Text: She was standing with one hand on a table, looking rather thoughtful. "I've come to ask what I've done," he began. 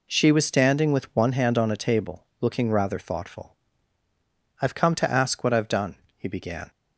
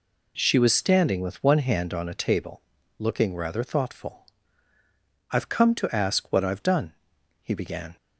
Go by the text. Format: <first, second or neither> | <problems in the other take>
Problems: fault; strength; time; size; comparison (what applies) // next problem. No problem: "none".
neither | none